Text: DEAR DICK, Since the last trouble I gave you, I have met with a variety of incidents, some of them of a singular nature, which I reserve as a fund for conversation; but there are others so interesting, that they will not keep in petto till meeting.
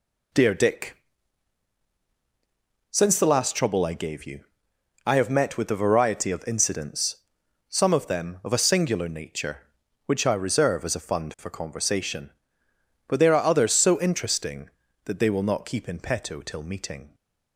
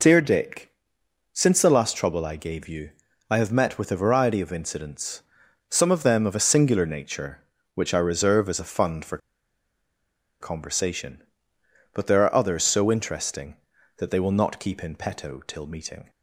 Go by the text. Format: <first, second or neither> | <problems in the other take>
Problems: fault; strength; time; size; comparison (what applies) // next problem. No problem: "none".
first | pauses between "for" and "conversation"; at 9.1 s; 1.2 s long